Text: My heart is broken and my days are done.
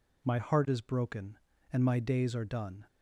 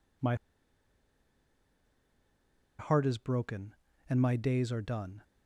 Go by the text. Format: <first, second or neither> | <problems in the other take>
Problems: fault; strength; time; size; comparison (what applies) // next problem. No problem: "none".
first | pauses between "My" and "heart"; strong; at 0.3 s; 2.4 s long